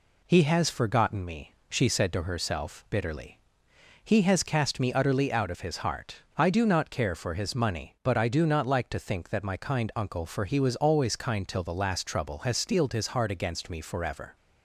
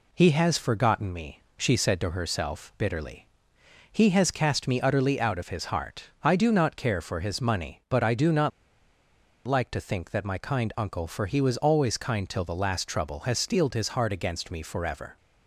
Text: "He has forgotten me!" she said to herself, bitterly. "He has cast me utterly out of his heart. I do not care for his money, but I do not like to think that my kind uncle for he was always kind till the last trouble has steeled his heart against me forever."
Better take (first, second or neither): first